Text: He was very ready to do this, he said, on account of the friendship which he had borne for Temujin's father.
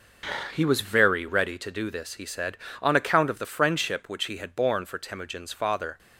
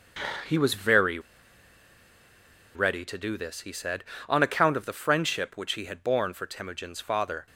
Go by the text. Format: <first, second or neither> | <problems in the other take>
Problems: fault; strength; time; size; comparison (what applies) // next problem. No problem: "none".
first | starts louder than the rest; until 3.0 s; 7 dB; also in the first // pauses between "very" and "ready"; strong; at 1.1 s; 1.5 s long